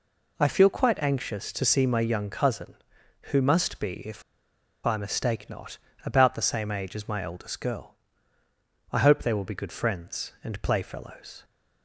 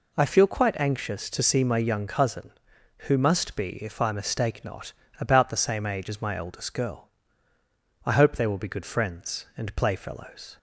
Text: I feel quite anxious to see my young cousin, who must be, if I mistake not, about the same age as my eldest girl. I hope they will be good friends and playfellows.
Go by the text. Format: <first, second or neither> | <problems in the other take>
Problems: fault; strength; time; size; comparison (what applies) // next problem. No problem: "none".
second | pauses between "if" and "I"; noticeable; at 4.2 s; 0.63 s long